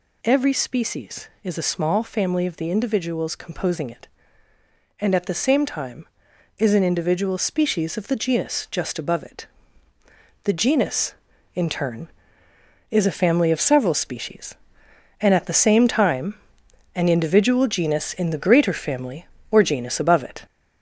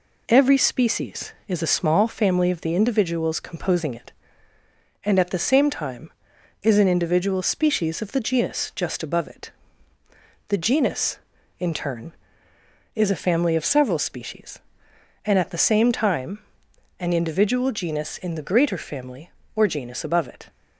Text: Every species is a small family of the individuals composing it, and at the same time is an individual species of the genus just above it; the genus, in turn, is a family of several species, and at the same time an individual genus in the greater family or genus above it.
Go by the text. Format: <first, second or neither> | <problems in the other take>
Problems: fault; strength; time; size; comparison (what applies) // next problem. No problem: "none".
second | gets louder; noticeable; throughout; 4.5 dB // pauses between "time" and "an"; noticeable; at 16.3 s; 0.58 s long; noticeable in the second